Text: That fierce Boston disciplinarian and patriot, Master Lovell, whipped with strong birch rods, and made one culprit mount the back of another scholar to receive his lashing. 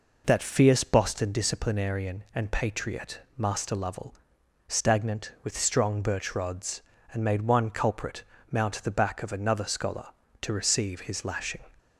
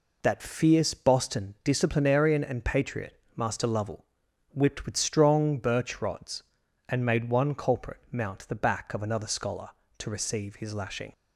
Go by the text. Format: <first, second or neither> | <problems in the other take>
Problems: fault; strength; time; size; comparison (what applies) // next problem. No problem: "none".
second | says "stagnant" for "whipped"; at 4.6 s // pauses between "culprit" and "mount"; slight; at 8.2 s; 0.26 s long